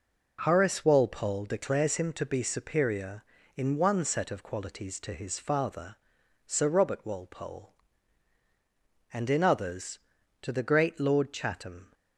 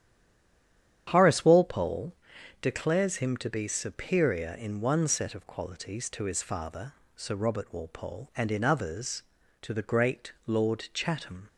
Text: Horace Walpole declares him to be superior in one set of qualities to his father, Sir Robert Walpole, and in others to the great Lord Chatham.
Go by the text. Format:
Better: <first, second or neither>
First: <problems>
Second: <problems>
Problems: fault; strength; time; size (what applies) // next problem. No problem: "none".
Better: first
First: none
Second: stays silent before the first word; until 1.0 s; 1.0 s long // starts louder than the rest; strong; until 2.1 s; 9.5 dB // pauses between "Walpole" and "declares"; noticeable; at 2.1 s; 0.48 s long